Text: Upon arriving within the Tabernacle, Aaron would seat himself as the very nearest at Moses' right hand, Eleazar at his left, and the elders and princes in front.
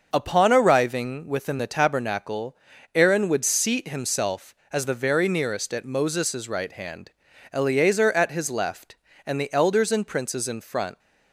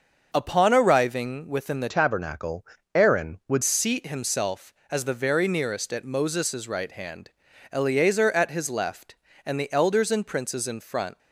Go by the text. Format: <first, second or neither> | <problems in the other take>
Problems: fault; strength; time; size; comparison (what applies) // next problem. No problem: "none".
first | starts louder than the rest; until 1.3 s; 6.5 dB; also in the first // changes voice from "Tabernacle" to "would"; from 1.8 to 3.6 s; 1.8 s long